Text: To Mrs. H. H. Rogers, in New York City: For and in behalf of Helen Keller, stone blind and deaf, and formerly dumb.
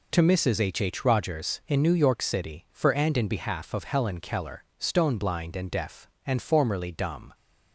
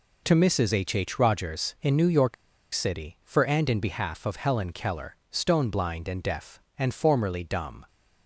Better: first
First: none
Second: pauses between "York" and "City"; at 2.3 s; 0.39 s long

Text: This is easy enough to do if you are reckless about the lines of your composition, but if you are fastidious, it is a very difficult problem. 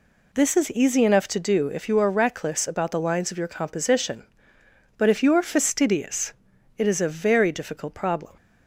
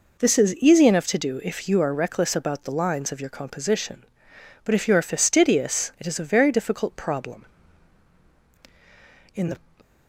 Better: first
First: none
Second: goes on to say "In the"; slight; from 9.3 s on; 0.28 s long

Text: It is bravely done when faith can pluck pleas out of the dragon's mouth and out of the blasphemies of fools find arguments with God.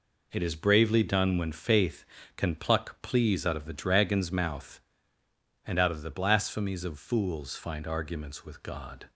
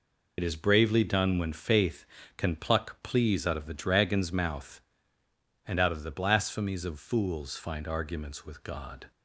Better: first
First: none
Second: loses the start of "It"; at 0.3 s; 55 ms

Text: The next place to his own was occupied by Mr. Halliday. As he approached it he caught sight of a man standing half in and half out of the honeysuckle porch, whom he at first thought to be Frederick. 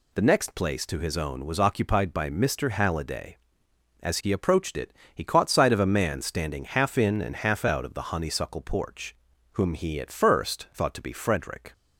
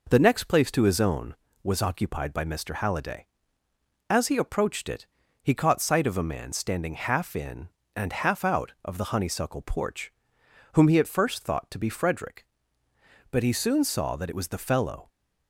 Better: first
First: pauses between "it" and "he"; slight; at 4.9 s; 0.20 s long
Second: pauses between "it" and "he"; slight; at 5.0 s; 0.34 s long // goes on to say "But he soon saw that it was the fellow"; strong; from 13.3 s on; 1.7 s long

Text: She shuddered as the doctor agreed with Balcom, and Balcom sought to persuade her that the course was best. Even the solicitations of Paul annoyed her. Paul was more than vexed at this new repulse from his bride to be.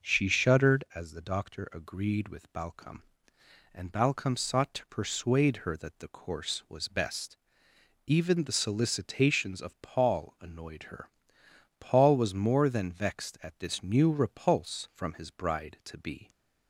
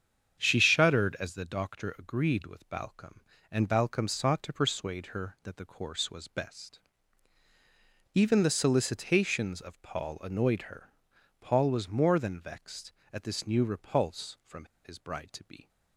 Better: first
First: none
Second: starts louder than the rest; strong; until 1.4 s; 8 dB // pauses between "from" and "his"; slight; at 14.6 s; 0.19 s long

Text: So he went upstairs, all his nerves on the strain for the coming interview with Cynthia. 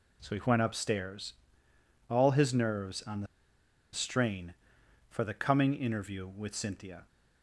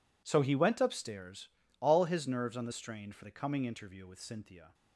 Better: second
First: pauses between "the" and "strain"; noticeable; at 3.2 s; 0.66 s long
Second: none

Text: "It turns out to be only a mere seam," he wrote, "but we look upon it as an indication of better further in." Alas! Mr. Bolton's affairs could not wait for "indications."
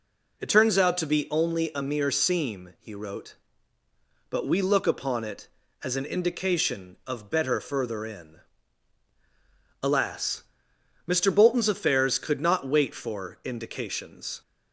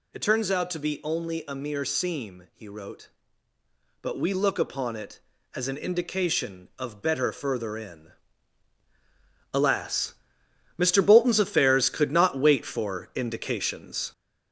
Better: first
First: none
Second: gets louder; noticeable; throughout; 4.5 dB

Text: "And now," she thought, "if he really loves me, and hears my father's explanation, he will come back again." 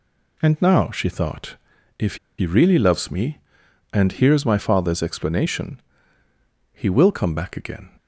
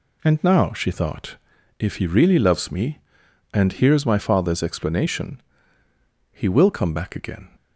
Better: second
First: pauses between "if" and "he"; slight; at 2.1 s; 0.21 s long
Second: none

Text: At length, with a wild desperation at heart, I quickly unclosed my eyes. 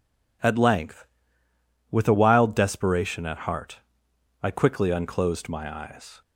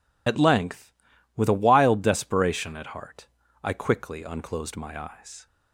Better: first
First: none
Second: loses the start of "At"; at 0.2 s; 50 ms

